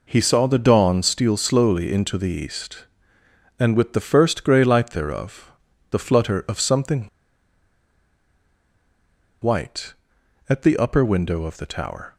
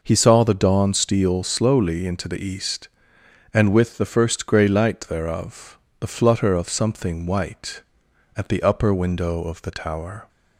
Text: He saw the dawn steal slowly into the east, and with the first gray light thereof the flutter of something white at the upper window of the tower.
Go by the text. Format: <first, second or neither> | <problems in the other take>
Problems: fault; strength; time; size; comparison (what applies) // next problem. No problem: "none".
second | pauses between "thereof" and "the"; at 5.5 s; 0.38 s long; slight in the second // pauses between "something" and "white"; strong; at 7.0 s; 2.4 s long